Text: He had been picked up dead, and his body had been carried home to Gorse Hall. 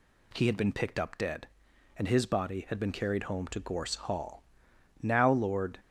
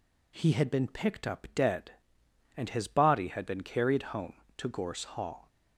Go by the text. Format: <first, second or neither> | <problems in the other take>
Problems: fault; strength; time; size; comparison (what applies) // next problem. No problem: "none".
second | goes on to say "Now Lord"; noticeable; from 5.0 s on; 0.78 s long